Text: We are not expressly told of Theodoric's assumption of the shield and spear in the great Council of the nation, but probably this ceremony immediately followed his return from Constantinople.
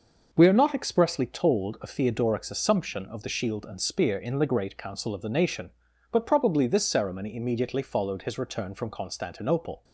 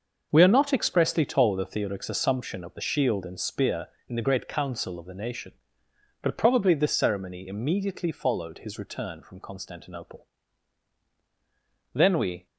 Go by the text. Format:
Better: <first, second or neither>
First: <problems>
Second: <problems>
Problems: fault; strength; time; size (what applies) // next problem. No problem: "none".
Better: first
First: none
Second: goes on to say "Then we"; from 11.9 s on; 0.52 s long